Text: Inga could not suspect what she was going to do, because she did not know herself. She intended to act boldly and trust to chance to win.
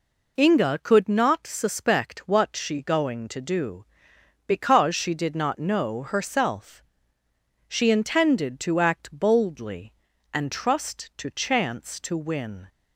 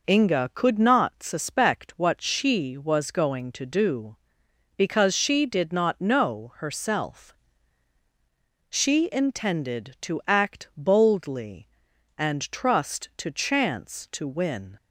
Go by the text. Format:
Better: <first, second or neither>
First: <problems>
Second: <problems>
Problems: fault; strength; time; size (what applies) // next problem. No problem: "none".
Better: second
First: skips "was"; at 2.8 s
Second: none